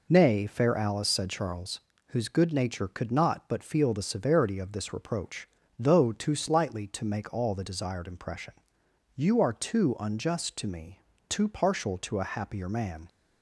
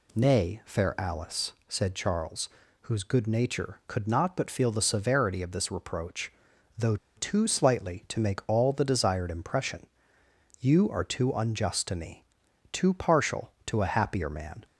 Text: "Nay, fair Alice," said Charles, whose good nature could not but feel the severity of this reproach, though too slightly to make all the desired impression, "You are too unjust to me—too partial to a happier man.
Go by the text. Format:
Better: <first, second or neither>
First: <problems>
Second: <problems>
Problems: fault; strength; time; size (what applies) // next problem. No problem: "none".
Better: first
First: none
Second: pauses between "though" and "too"; slight; at 6.9 s; 0.20 s long